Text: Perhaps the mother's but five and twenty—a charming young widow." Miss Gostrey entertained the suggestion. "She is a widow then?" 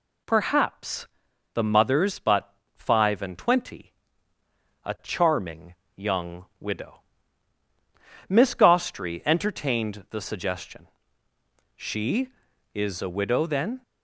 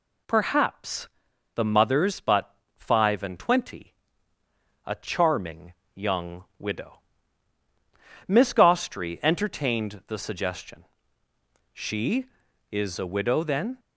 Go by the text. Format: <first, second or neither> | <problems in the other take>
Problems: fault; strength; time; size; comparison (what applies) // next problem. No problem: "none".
neither | pauses between "Perhaps" and "the"; noticeable; the same in both // pauses between "but" and "five"; slight; the same in both // pauses between "charming" and "young"; slight; the same in both